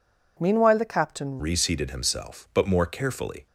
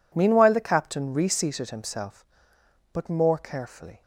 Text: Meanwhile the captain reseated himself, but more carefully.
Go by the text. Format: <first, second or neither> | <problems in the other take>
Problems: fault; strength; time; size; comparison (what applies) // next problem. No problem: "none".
second | changes voice at "reseated"; from 1.3 s on; 2.1 s long